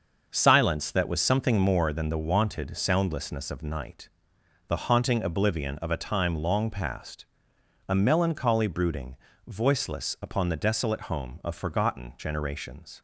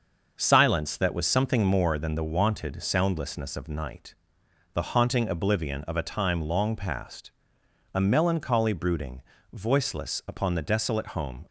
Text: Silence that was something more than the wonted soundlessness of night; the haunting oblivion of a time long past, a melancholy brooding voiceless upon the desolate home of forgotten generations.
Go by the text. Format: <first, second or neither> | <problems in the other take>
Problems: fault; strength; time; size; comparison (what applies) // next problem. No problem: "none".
first | starts louder than the rest; until 1.3 s; 6.5 dB; also in the first // pauses between "brooding" and "voiceless"; slight; at 9.2 s; 0.30 s long; slight in the first // stops before "of forgotten generations"; at 11.4 s